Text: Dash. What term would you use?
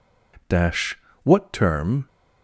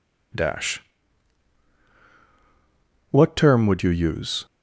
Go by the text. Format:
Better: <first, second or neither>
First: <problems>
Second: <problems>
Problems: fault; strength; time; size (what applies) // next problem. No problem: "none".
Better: second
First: stops before "would you use"; at 2.0 s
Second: none